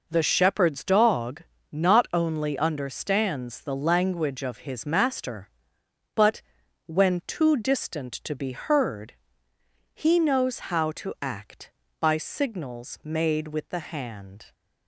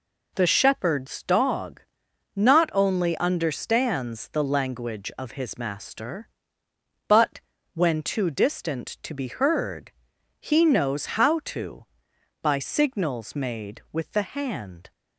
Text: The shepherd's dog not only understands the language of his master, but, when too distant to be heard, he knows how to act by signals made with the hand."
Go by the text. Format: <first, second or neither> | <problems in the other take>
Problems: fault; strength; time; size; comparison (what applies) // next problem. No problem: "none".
first | pauses between "dog" and "not"; noticeable; at 1.8 s; 0.56 s long; slight in the first // skips "act"; at 12.1 s